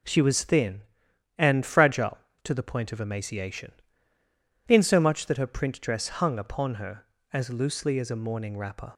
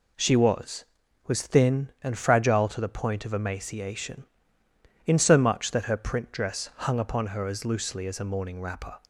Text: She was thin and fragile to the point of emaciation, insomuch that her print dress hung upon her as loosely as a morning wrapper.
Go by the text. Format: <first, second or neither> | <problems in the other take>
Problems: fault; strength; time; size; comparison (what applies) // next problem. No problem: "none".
first | says "was" twice; at 1.2 s